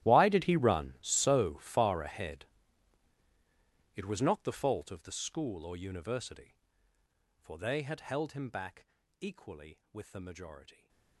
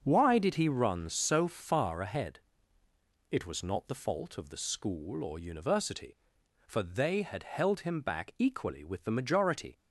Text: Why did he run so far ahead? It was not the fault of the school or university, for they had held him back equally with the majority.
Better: second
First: gets quieter; strong; throughout; 19.5 dB // starts louder than the rest; strong; until 1.0 s; 13.5 dB // pauses between "back" and "equally"; slight; at 8.8 s; 0.36 s long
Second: starts louder than the rest; until 1.0 s; 6.5 dB

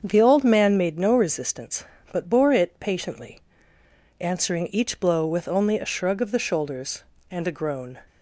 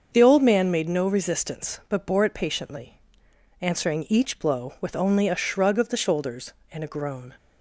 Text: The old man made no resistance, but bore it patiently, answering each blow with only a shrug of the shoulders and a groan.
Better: neither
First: starts louder than the rest; until 1.0 s; 7 dB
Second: starts louder than the rest; until 1.1 s; 6.5 dB

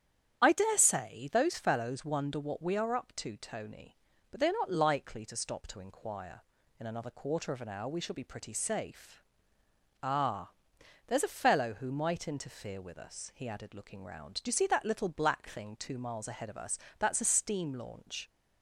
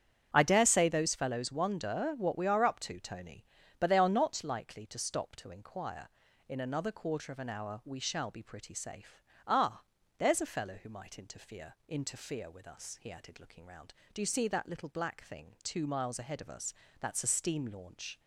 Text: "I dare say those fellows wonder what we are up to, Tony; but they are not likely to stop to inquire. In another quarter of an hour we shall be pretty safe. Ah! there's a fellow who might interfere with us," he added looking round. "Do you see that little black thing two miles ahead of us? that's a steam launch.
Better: first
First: starts louder than the rest; strong; until 1.4 s; 9.5 dB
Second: starts louder than the rest; strong; until 1.3 s; 8.5 dB // says "interfere" twice; at 11.8 s

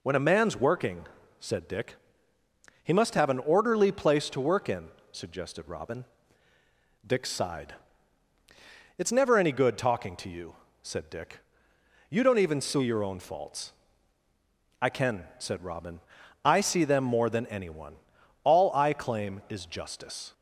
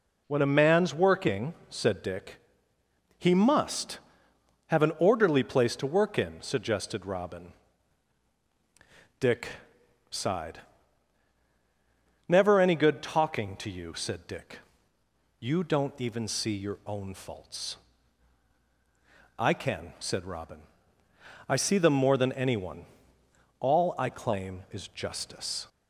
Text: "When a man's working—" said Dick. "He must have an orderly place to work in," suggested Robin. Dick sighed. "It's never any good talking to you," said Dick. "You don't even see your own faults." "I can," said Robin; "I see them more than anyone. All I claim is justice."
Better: first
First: none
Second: pauses between "Dick" and "sighed"; noticeable; at 9.4 s; 0.60 s long // skips "It's"; at 11.4 s

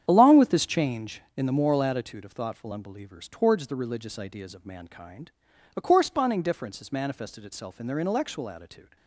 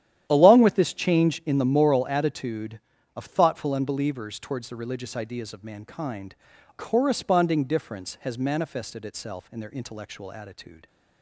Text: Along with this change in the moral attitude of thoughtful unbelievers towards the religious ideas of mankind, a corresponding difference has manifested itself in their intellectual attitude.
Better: first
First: starts louder than the rest; strong; until 1.0 s; 9 dB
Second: starts louder than the rest; strong; until 1.3 s; 11 dB // skips "a"; at 6.5 s

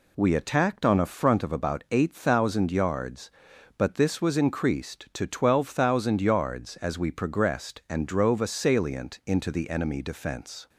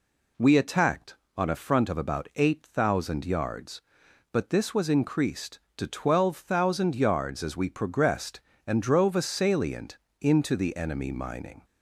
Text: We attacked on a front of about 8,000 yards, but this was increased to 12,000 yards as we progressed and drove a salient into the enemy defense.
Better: first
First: none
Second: pauses between "salient" and "into"; slight; at 9.9 s; 0.22 s long // says "mining" for "defense"; at 11.1 s

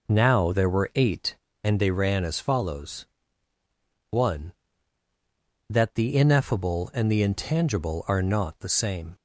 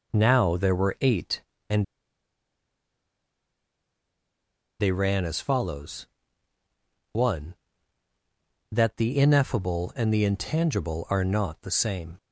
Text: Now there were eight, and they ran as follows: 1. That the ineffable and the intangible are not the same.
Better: first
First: none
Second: pauses between "and" and "they"; strong; at 1.8 s; 2.9 s long

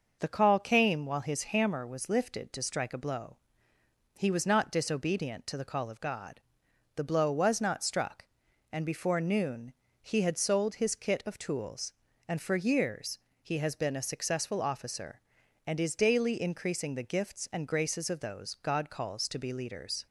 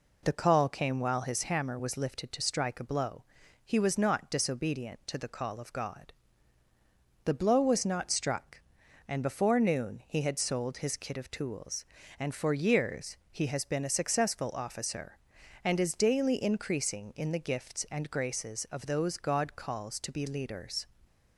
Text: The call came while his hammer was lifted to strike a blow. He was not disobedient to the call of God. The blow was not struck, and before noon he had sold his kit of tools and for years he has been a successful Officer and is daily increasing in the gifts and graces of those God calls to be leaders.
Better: second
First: pauses between "noon" and "he"; slight; at 9.7 s; 0.28 s long // pauses between "years" and "he"; slight; at 13.1 s; 0.22 s long // skips "in"; at 16.9 s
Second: pauses between "years" and "he"; slight; at 13.1 s; 0.16 s long

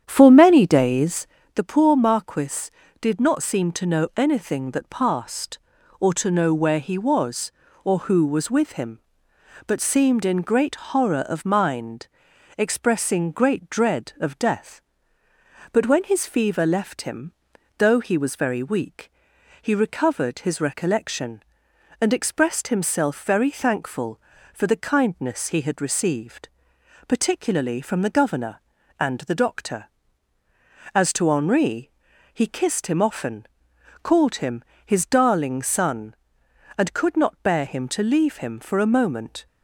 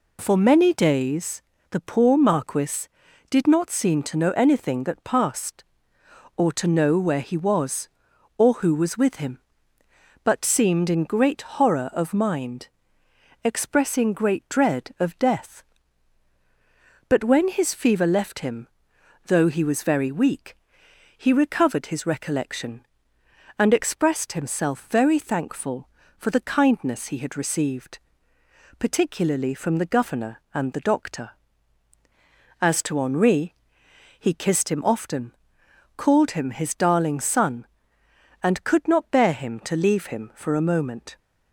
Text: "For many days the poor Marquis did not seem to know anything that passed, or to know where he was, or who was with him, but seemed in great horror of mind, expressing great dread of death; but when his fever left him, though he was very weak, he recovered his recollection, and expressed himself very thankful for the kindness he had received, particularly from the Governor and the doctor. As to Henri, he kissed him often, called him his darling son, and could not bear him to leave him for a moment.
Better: second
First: starts louder than the rest; strong; until 1.4 s; 9 dB // pauses between "days" and "the"; slight; at 1.2 s; 0.28 s long // pauses between "him" and "his"; slight; at 34.6 s; 0.24 s long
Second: pauses between "days" and "the"; slight; at 1.3 s; 0.30 s long

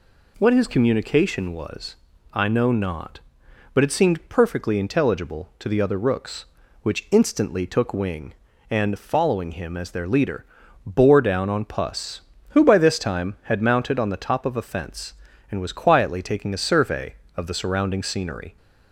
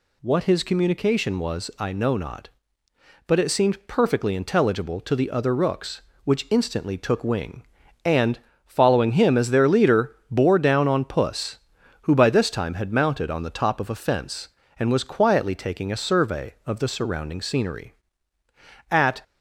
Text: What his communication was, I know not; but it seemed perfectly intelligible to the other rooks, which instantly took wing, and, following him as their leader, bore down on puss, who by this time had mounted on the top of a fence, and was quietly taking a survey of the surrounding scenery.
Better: first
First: none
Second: goes on to say "At"; slight; from 18.9 s on; 0.30 s long

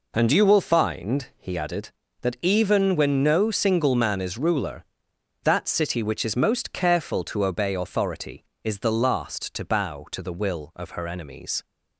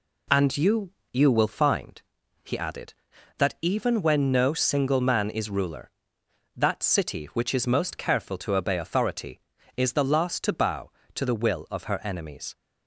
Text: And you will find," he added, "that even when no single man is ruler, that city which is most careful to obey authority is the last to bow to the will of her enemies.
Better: first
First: none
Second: says "you" twice; at 1.1 s

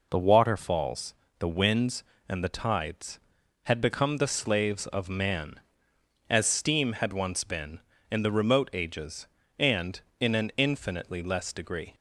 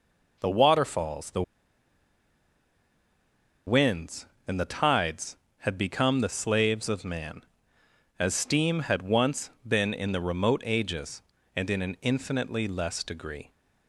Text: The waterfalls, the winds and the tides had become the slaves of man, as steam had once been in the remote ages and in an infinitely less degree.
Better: first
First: none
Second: pauses between "the" and "winds"; strong; at 1.4 s; 2.2 s long // pauses between "once" and "been"; slight; at 9.5 s; 0.16 s long

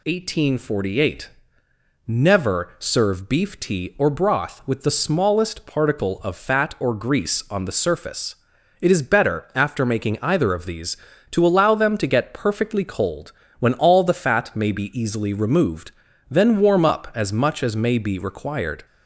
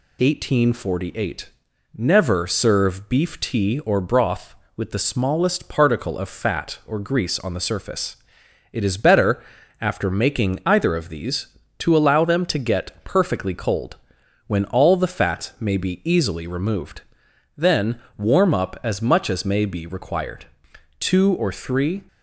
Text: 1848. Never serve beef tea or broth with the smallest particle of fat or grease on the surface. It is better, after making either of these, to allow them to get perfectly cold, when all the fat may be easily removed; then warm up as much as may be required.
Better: first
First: none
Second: pauses between "then" and "warm"; slight; at 17.9 s; 0.20 s long // goes on to say "Two or three"; noticeable; from 20.9 s on; 1.0 s long

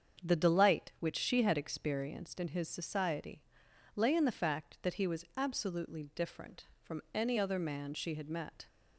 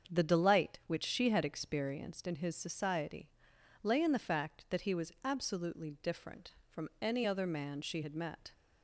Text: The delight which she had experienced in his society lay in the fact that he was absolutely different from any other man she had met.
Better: neither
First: starts louder than the rest; strong; until 1.3 s; 7 dB // pauses between "society" and "lay"; noticeable; at 3.4 s; 0.54 s long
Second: starts louder than the rest; until 1.1 s; 7 dB // pauses between "society" and "lay"; noticeable; at 3.2 s; 0.54 s long

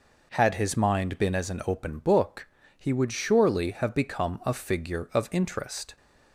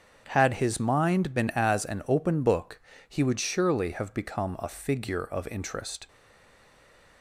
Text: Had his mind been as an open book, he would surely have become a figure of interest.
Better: first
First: none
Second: starts louder than the rest; strong; until 1.3 s; 7.5 dB // stays silent after the last word; from 6.0 s on; 1.2 s long

